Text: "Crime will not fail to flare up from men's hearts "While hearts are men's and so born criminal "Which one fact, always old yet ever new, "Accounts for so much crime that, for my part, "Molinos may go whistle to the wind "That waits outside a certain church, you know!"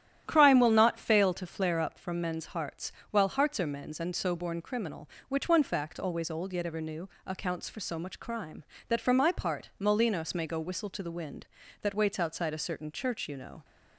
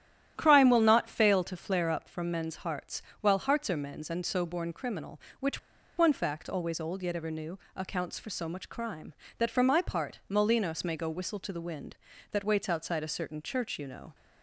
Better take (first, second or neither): first